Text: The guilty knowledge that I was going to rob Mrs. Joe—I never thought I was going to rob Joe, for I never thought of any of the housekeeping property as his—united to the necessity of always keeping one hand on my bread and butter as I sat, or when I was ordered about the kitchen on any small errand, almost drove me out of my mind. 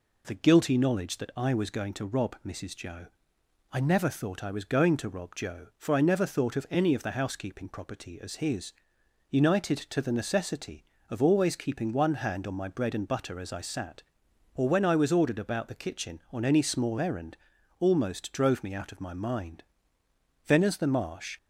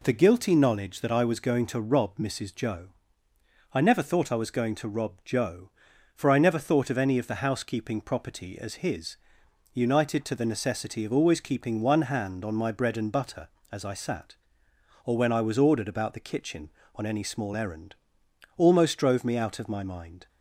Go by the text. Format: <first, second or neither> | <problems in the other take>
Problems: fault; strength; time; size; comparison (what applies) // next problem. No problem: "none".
second | goes on to say "Then as the marsh"; noticeable; from 20.4 s on; 0.90 s long